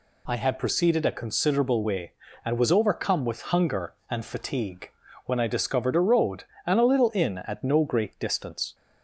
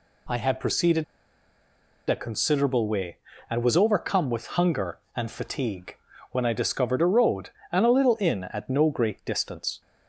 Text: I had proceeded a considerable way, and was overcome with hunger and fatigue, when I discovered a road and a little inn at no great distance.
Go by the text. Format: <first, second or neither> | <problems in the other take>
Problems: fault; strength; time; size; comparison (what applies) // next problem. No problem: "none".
first | pauses between "proceeded" and "a"; at 1.0 s; 1.0 s long